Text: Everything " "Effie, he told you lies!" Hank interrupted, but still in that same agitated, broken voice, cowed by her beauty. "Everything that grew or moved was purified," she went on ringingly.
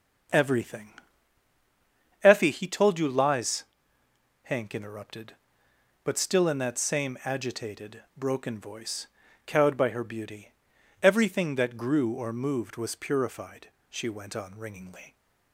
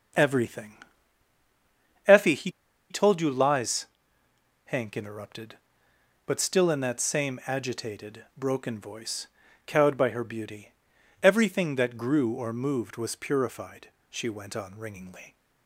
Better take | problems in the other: first | pauses between "he" and "told"; at 2.4 s; 0.40 s long

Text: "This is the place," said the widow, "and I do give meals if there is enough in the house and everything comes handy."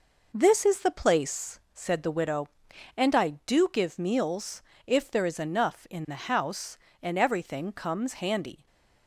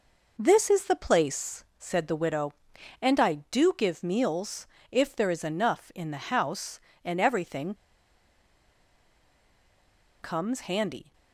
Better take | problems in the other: first | pauses between "meals" and "if"; slight; at 4.6 s; 0.24 s long; slight in the first // pauses between "everything" and "comes"; strong; at 7.7 s; 2.4 s long

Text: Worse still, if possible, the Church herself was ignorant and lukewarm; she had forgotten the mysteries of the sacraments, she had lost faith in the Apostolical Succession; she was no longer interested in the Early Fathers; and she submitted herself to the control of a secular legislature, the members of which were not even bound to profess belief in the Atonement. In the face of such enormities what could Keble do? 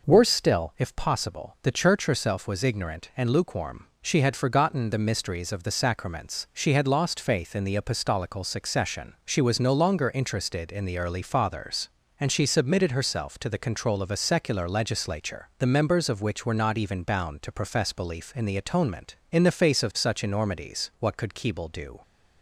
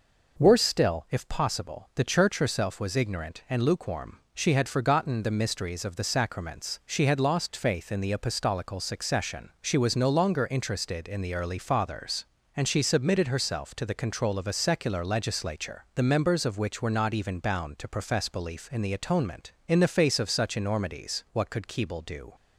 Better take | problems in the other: neither | none

